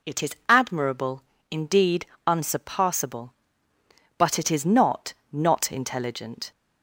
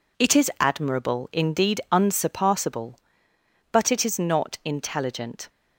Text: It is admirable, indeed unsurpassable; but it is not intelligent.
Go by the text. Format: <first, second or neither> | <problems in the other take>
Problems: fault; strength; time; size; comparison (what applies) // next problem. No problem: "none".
second | pauses between "indeed" and "unsurpassable"; slight; at 2.0 s; 0.22 s long // says "not" twice; at 5.3 s